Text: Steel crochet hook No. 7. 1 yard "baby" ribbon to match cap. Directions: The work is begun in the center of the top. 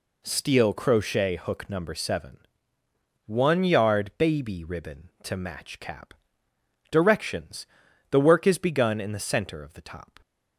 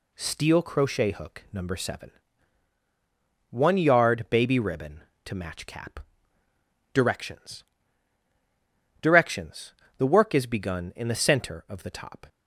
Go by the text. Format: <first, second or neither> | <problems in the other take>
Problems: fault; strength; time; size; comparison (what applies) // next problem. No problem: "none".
first | says "Directions" twice; at 9.0 s